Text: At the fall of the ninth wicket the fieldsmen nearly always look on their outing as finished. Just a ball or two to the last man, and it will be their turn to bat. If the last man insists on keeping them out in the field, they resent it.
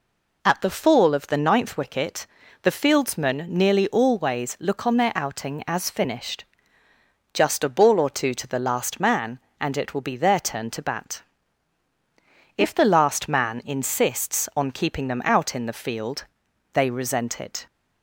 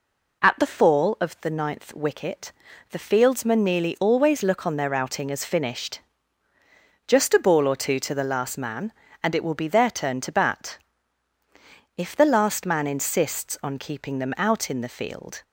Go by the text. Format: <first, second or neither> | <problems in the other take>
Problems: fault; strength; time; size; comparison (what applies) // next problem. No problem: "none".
first | pauses between "wicket" and "the"; at 2.5 s; 0.38 s long; slight in the first // stops before "they resent it"; at 15.4 s